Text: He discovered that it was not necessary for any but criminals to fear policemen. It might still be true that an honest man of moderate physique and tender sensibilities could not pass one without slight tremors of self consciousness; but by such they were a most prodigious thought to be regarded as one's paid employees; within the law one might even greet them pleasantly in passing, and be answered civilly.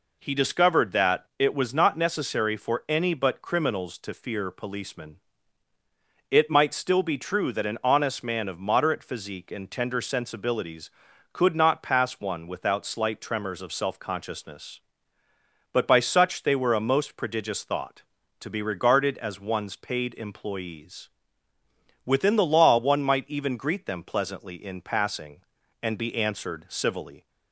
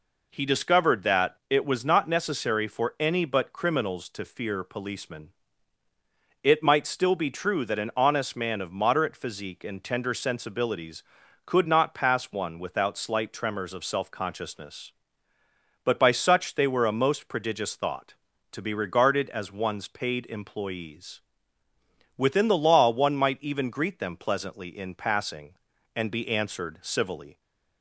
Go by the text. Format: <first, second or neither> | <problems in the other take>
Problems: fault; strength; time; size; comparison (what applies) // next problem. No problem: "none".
neither | none